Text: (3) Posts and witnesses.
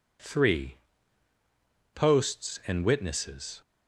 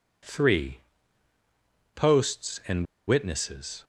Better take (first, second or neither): first